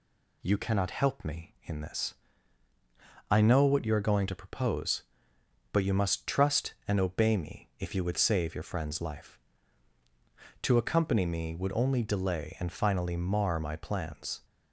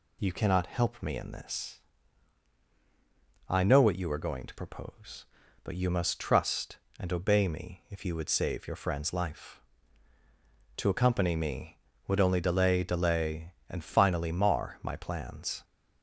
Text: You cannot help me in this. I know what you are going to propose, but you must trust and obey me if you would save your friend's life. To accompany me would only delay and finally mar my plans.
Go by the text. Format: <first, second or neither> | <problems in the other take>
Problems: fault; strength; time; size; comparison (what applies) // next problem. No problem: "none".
first | says "delay" twice; at 12.8 s